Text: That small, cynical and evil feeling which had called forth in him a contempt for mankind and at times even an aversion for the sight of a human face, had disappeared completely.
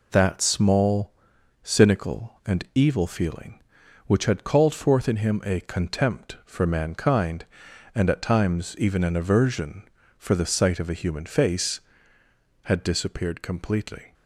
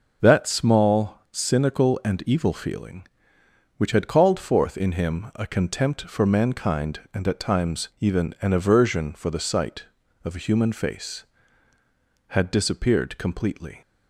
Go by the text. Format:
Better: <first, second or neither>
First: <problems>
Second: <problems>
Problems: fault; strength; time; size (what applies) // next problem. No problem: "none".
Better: neither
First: none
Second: none